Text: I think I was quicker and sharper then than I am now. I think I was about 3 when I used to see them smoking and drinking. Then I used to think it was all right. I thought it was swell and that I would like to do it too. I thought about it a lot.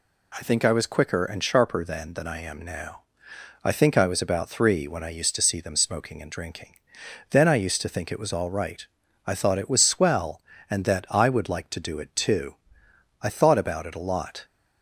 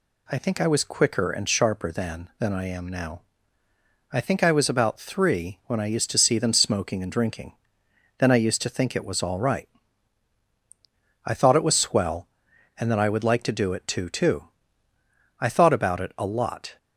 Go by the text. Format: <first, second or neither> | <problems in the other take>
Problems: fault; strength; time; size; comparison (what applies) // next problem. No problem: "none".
first | says "too" twice; at 14.0 s